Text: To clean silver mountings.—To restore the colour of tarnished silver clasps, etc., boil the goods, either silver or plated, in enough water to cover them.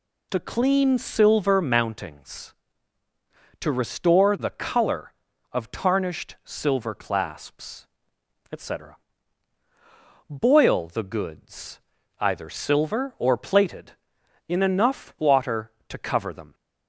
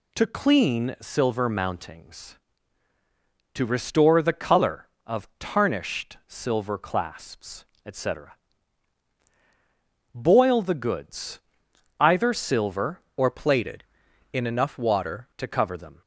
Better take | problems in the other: first | changes voice from "or" to "water"; from 13.1 to 15.2 s; 2.1 s long

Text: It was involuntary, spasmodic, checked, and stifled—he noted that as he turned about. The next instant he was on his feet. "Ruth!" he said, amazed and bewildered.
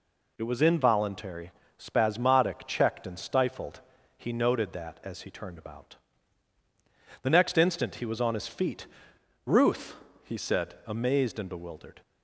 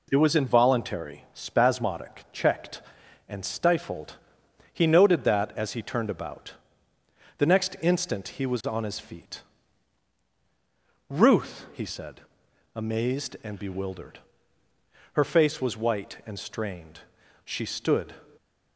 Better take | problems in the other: first | goes on to say "Her face was white and strained She stood"; strong; from 15.1 s on; 3.0 s long

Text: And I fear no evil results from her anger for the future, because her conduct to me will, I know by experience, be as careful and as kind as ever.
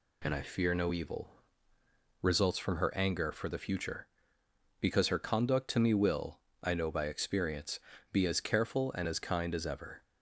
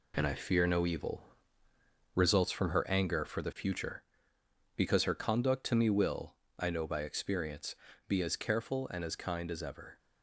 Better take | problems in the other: first | gets quieter; strong; throughout; 7.5 dB // pauses between "evil" and "results"; noticeable; at 1.2 s; 0.92 s long; noticeable in the first

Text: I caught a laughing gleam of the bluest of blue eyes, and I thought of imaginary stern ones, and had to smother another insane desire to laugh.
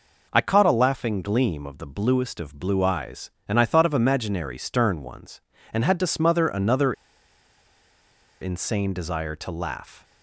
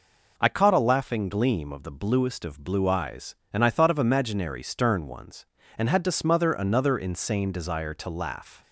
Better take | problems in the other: second | pauses between "another" and "insane"; strong; at 6.9 s; 1.4 s long

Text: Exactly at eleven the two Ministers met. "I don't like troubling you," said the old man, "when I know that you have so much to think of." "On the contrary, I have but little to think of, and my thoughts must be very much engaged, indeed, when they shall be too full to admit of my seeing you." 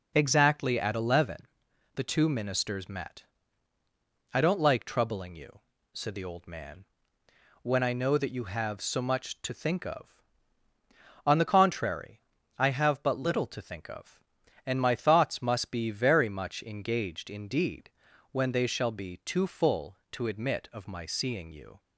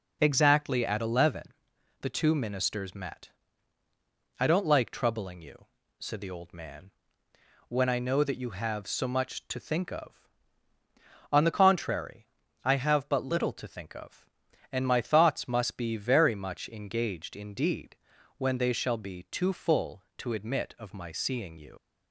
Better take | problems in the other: first | pauses between "eleven" and "the"; noticeable; at 1.4 s; 0.58 s long; noticeable in the first // leaves "you" unfinished; at 21.7 s; 75 ms

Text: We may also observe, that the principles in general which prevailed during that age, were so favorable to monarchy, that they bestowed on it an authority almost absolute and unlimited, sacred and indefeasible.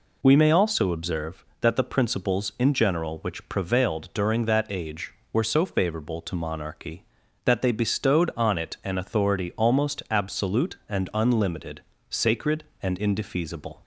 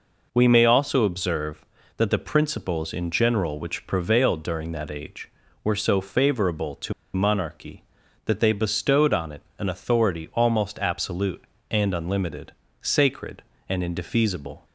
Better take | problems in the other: first | pauses between "to" and "monarchy"; slight; at 6.9 s; 0.21 s long // pauses between "it" and "an"; slight; at 9.4 s; 0.16 s long

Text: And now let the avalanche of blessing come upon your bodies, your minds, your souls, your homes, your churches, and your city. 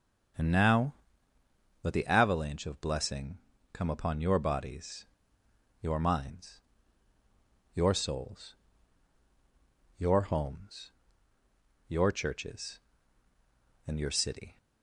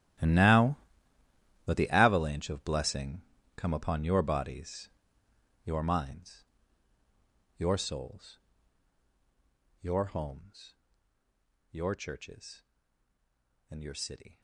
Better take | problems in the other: first | gets quieter; strong; throughout; 18 dB // starts louder than the rest; strong; until 2.1 s; 13.5 dB; strong in the first // pauses between "now" and "let"; noticeable; at 0.7 s; 0.90 s long; noticeable in the first // pauses between "blessing" and "come"; slight; at 3.2 s; 0.36 s long; slight in the first

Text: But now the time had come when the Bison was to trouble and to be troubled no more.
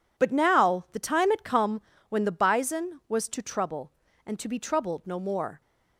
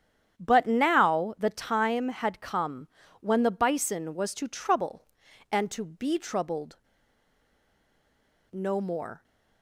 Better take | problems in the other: first | starts louder than the rest; strong; until 1.4 s; 9 dB // pauses between "come" and "when"; slight; at 2.8 s; 0.32 s long; slight in the first // pauses between "troubled" and "no"; strong; at 6.7 s; 1.7 s long

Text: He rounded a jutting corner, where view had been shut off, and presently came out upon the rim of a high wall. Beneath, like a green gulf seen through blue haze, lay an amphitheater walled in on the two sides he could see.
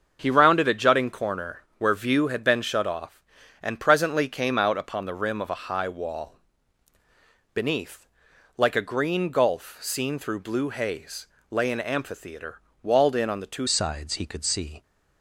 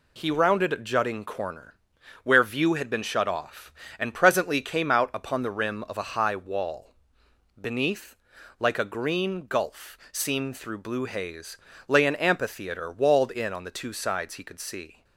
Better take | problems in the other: second | starts louder than the rest; until 1.2 s; 6.5 dB // pauses between "amphitheater" and "walled"; slight; at 12.6 s; 0.22 s long // changes voice at "sides"; from 13.6 s on; 1.2 s long

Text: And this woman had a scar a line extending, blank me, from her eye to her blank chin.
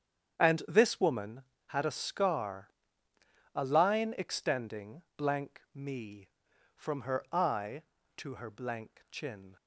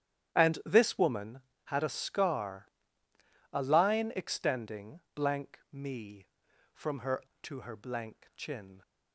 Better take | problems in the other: first | starts louder than the rest; strong; until 1.6 s; 11 dB; strong in the first // pauses between "scar" and "a"; noticeable; at 2.6 s; 0.86 s long; noticeable in the first // skips "eye"; at 7.3 s

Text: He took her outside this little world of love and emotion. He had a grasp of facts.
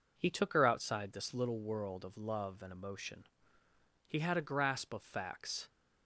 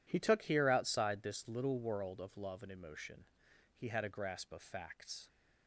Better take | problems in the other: first | says "here" for "her"; at 0.4 s

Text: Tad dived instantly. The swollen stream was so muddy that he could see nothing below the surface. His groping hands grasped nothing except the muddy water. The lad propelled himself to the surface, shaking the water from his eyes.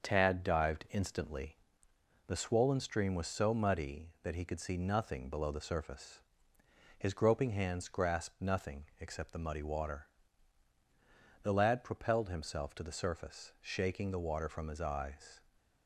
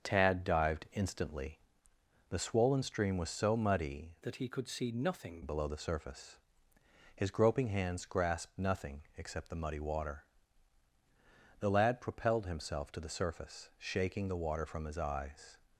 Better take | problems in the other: first | starts louder than the rest; until 1.0 s; 7 dB; also in the first // changes voice from "that" to "nothing"; from 4.2 to 5.4 s; 1.2 s long

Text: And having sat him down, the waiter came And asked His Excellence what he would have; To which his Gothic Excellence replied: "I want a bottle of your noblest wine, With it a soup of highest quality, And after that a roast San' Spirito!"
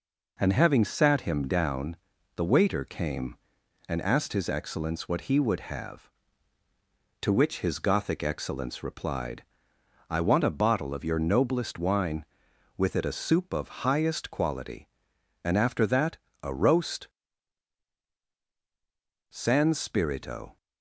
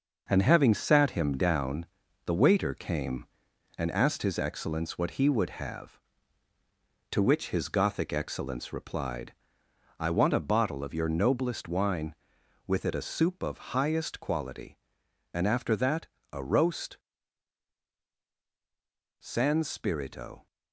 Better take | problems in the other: first | gets quieter; throughout; 6.5 dB // pauses between "that" and "a"; slight; at 16.0 s; 0.26 s long; slight in the first // pauses between "roast" and "San"; strong; at 16.9 s; 2.2 s long; strong in the first

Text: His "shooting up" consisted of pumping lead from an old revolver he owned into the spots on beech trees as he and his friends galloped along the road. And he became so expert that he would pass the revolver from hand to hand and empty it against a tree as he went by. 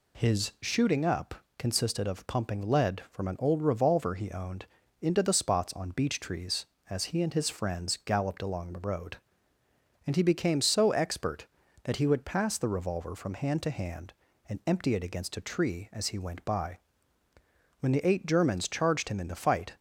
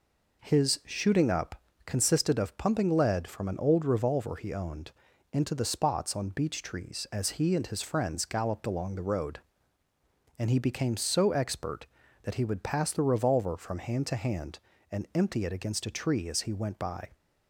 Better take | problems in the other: second | pauses between "up" and "consisted"; slight; at 1.3 s; 0.24 s long; slight in the second // pauses between "owned" and "into"; at 4.6 s; 0.38 s long; also in the second // goes on to say "When the eight Germans charged him in the fight"; strong; from 17.7 s on; 1.9 s long

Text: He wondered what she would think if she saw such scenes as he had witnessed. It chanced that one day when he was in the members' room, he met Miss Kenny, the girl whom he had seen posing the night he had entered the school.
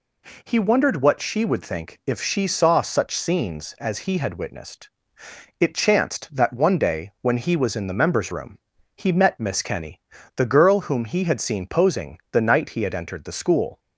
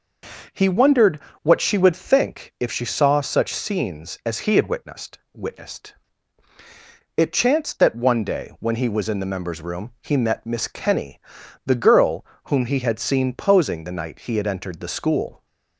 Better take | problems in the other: first | pauses between "wondered" and "what"; slight; at 1.2 s; 0.22 s long // says "witnessed" twice; at 5.3 s // pauses between "girl" and "whom"; slight; at 12.2 s; 0.24 s long

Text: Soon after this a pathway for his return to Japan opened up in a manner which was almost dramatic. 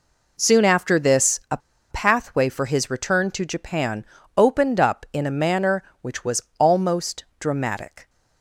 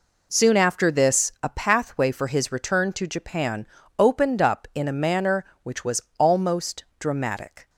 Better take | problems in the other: second | pauses between "a" and "pathway"; slight; at 1.5 s; 0.32 s long // pauses between "Japan" and "opened"; slight; at 4.0 s; 0.32 s long; slight in the second // pauses between "was" and "almost"; slight; at 6.4 s; 0.18 s long; slight in the second // pauses between "almost" and "dramatic"; slight; at 7.2 s; 0.16 s long; slight in the second

